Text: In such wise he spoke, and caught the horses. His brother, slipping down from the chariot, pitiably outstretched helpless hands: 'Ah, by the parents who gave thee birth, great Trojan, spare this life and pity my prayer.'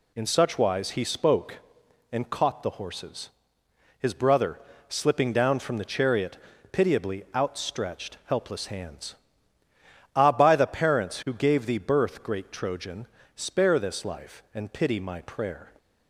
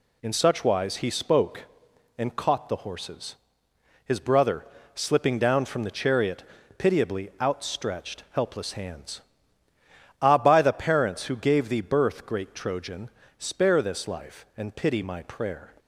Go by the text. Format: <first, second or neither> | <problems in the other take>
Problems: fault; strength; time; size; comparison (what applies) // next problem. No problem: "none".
neither | none